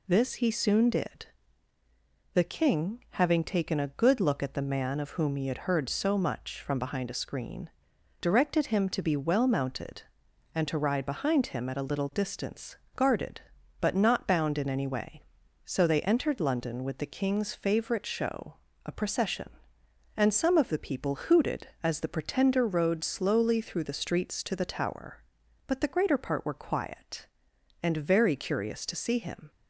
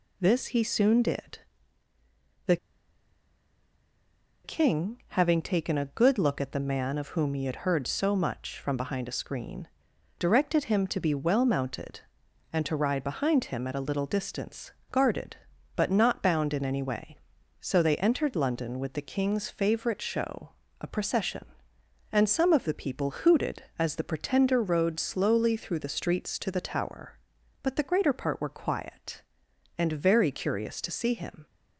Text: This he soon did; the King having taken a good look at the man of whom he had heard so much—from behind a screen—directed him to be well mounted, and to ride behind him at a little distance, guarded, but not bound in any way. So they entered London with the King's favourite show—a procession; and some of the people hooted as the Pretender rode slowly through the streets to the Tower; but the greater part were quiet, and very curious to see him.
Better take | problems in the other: first | pauses between "the" and "King"; strong; at 2.5 s; 1.8 s long

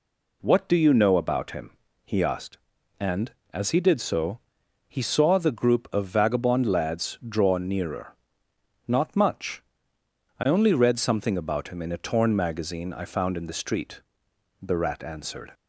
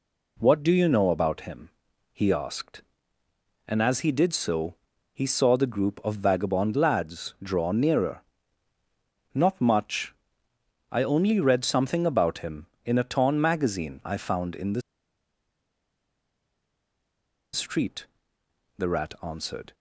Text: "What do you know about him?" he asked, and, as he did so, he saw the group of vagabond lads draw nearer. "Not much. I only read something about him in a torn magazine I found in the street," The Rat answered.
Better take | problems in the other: first | pauses between "the" and "street"; strong; at 14.8 s; 2.7 s long

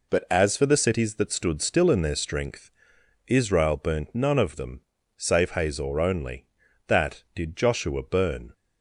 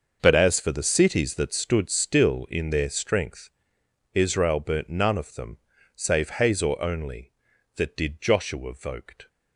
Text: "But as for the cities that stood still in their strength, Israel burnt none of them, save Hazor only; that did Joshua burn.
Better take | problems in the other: first | starts louder than the rest; until 1.2 s; 6.5 dB // says "voked" for "burn"; at 8.7 s

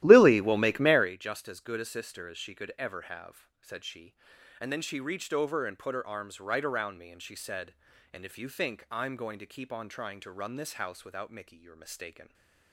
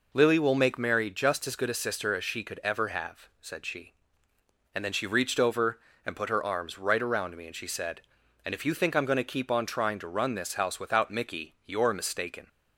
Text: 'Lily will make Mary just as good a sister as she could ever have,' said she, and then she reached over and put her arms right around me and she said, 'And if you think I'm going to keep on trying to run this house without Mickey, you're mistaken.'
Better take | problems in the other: second | starts louder than the rest; strong; until 1.2 s; 14 dB // stays silent after the last word; slight; from 12.2 s on; 0.5 s long

